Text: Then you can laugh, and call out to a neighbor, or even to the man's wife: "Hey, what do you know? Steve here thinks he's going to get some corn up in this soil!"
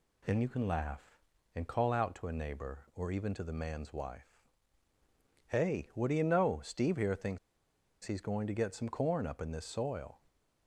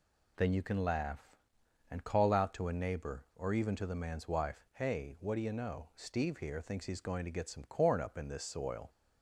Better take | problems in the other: second | pauses between "thinks" and "he's"; noticeable; at 7.3 s; 0.66 s long

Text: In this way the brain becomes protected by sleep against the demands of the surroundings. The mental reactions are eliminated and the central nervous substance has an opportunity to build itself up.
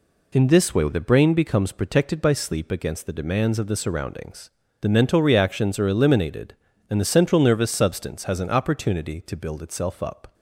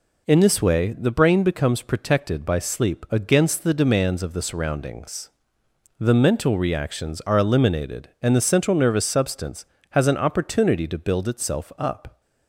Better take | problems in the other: neither | none

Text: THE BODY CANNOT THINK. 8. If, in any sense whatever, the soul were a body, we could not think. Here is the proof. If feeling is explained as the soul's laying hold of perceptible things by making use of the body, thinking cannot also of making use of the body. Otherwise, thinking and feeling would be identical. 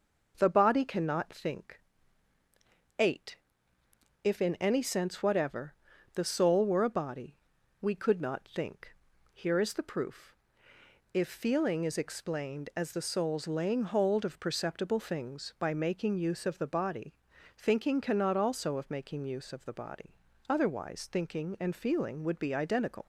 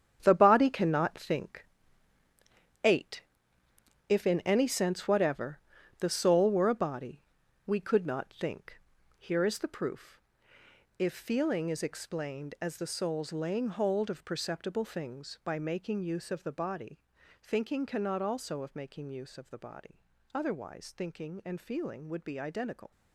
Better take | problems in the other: first | gets quieter; strong; throughout; 10 dB

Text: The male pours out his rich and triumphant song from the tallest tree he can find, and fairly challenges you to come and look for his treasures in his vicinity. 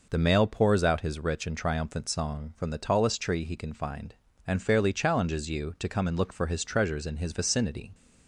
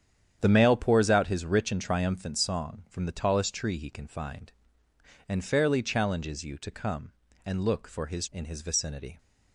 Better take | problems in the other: first | starts louder than the rest; strong; until 1.4 s; 9 dB // skips "treasures"; at 8.2 s

